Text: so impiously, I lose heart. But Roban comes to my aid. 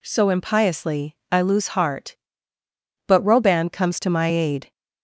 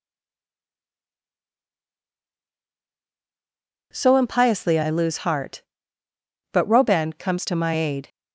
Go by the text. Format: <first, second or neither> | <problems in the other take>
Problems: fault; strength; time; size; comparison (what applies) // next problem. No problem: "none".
first | stays silent before the first word; strong; until 3.9 s; 3.9 s long